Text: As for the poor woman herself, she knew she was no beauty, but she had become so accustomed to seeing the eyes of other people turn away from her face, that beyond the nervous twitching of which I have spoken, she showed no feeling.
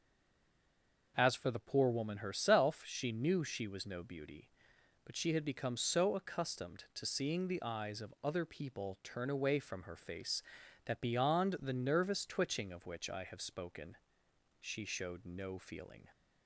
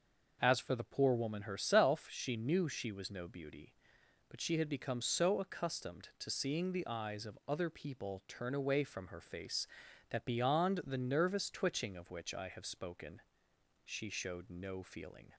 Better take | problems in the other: second | stays silent before the first word; until 1.1 s; 1.1 s long

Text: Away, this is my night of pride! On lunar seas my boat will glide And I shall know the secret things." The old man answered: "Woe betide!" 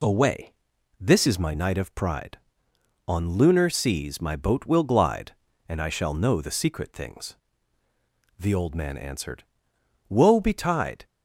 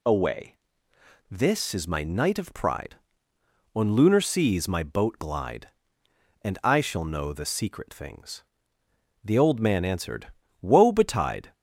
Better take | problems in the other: first | skips "will"; at 5.1 s

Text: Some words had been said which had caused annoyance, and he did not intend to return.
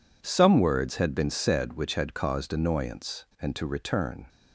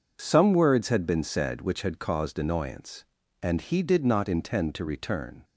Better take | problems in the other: second | skips "he did not intend"; at 3.5 s

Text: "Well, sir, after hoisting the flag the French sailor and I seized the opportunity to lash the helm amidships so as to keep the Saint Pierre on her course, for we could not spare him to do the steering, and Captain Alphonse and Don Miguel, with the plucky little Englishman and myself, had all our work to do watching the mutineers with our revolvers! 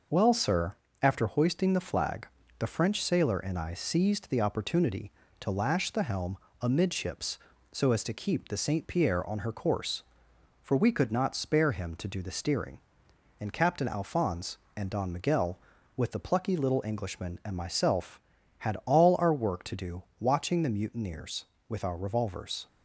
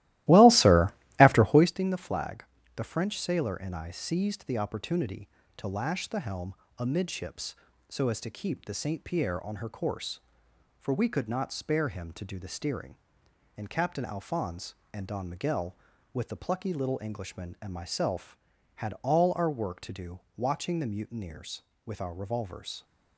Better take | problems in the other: first | starts louder than the rest; strong; until 1.8 s; 16.5 dB // pauses between "flag" and "the"; slight; at 2.4 s; 0.32 s long; slight in the first // pauses between "helm" and "amidships"; slight; at 6.5 s; 0.24 s long; slight in the first // pauses between "do" and "watching"; slight; at 20.1 s; 0.16 s long; slight in the first

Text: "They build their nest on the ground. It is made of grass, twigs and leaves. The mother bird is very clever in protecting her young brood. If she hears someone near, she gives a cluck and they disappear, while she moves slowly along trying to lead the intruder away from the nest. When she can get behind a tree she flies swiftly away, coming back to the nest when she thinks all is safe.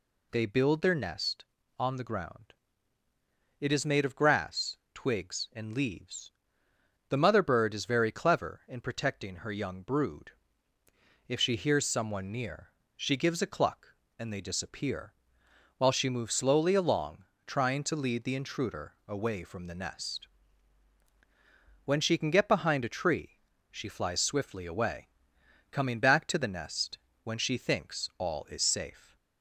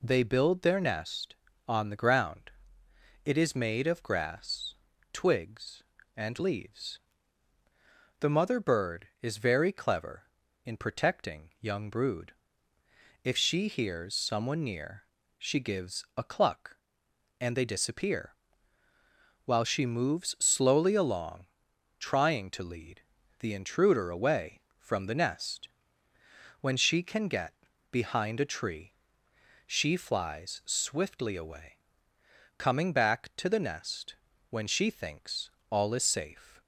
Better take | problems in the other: first | skips "her"; at 11.5 s // pauses between "along" and "trying"; noticeable; at 21.4 s; 0.54 s long; slight in the first // pauses between "lead" and "the"; slight; at 23.0 s; 0.36 s long // pauses between "get" and "behind"; at 27.5 s; 0.38 s long // pauses between "tree" and "she"; noticeable; at 28.8 s; 0.76 s long; slight in the first // pauses between "nest" and "when"; slight; at 34.1 s; 0.34 s long; slight in the first // pauses between "thinks" and "all"; slight; at 35.4 s; 0.22 s long

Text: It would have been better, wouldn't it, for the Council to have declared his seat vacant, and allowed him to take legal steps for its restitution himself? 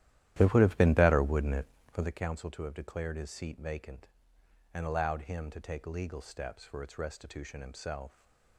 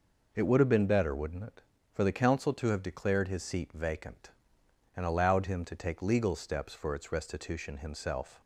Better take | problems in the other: second | starts louder than the rest; strong; until 2.2 s; 13 dB

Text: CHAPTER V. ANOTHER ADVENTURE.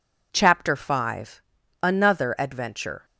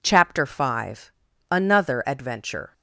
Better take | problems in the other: neither | none

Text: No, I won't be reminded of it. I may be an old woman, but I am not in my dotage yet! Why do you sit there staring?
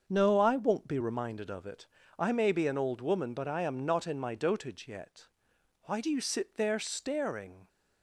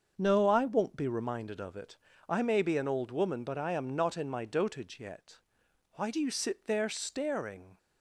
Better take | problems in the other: neither | starts louder than the rest; the same in both

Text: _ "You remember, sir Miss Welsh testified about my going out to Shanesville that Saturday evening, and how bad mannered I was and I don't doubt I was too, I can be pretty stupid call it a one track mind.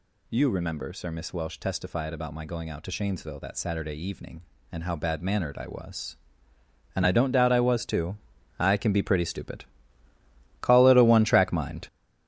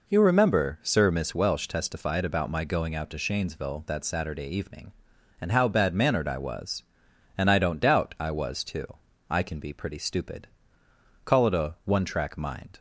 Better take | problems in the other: second | gets louder; strong; throughout; 9 dB // pauses between "stupid" and "call"; noticeable; at 9.6 s; 0.98 s long; noticeable in the second

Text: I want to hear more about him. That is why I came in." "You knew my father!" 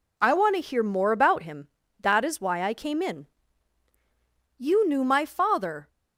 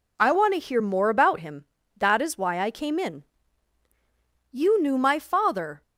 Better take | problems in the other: neither | none

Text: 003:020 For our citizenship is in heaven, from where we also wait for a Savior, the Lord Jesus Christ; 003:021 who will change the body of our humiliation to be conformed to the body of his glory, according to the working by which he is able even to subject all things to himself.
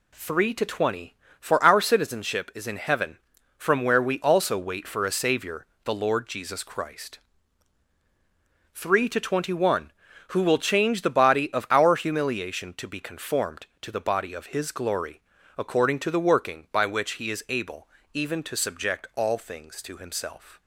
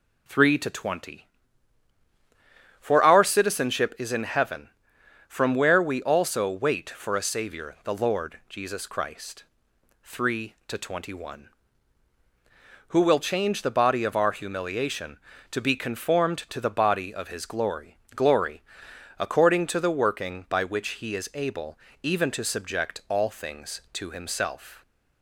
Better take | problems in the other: first | says "glory" twice; at 18.1 s // pauses between "able" and "even"; slight; at 21.7 s; 0.24 s long; slight in the first

